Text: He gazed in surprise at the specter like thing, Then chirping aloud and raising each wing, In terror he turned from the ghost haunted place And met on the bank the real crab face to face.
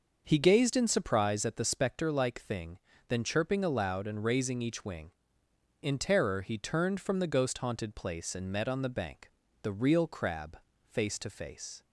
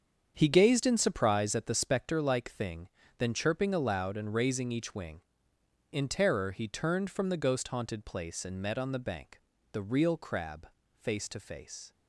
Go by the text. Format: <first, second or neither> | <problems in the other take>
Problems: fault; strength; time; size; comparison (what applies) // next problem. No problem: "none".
first | gets quieter; strong; throughout; 11.5 dB // starts louder than the rest; strong; until 1.3 s; 7.5 dB; noticeable in the first // pauses between "bank" and "the"; slight; at 9.3 s; 0.32 s long; slight in the first // pauses between "crab" and "face"; slight; at 10.6 s; 0.26 s long; slight in the first